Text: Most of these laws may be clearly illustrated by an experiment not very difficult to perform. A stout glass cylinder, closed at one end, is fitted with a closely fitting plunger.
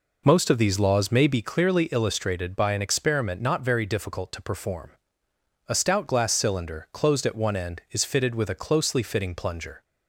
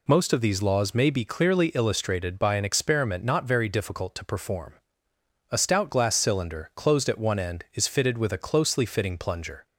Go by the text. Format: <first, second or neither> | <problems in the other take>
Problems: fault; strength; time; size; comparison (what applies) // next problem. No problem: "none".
second | starts louder than the rest; noticeable; until 1.5 s; 4.5 dB